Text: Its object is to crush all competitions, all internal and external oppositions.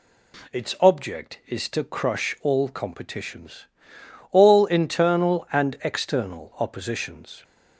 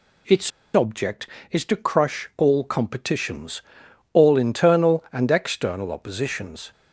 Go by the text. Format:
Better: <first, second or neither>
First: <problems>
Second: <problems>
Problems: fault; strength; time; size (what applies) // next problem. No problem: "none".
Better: first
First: none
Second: pauses between "Its" and "object"; slight; at 0.4 s; 0.24 s long